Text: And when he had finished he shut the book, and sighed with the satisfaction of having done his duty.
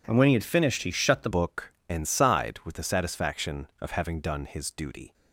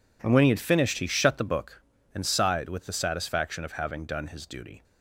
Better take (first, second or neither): second